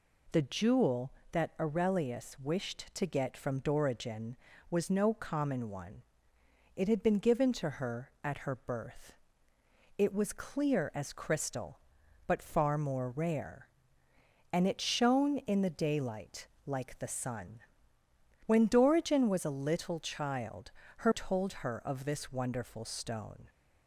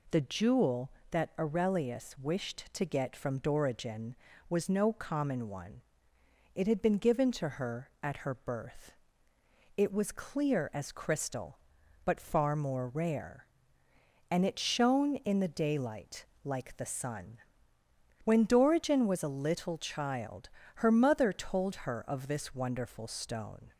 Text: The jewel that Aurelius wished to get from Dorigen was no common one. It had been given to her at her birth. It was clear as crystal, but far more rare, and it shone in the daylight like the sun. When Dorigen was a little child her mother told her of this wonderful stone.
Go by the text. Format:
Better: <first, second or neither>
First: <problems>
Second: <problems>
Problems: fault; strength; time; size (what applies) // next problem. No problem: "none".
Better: second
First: pauses between "daylight" and "like"; slight; at 16.4 s; 0.18 s long // pauses between "child" and "her"; slight; at 20.7 s; 0.26 s long // skips "mother"; at 21.1 s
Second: pauses between "daylight" and "like"; slight; at 16.2 s; 0.18 s long // pauses between "child" and "her"; slight; at 20.4 s; 0.26 s long